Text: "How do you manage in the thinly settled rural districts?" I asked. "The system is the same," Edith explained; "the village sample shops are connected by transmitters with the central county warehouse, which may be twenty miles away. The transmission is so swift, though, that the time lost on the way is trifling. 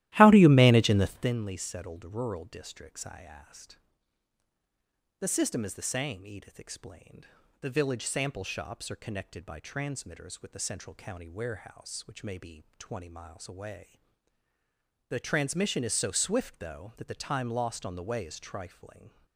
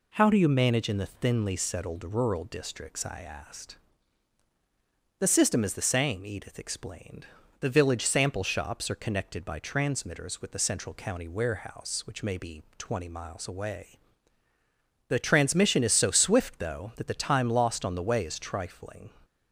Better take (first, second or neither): second